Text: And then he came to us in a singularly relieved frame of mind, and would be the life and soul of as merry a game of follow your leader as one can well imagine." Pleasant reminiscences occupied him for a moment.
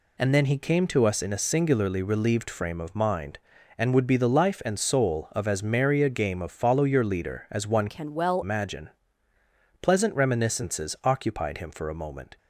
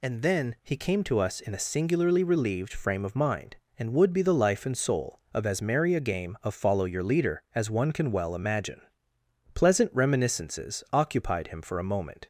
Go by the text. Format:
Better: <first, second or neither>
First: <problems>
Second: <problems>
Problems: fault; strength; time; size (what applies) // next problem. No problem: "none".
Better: second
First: changes voice from "can" to "well"; from 7.8 to 8.4 s; 0.6 s long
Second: none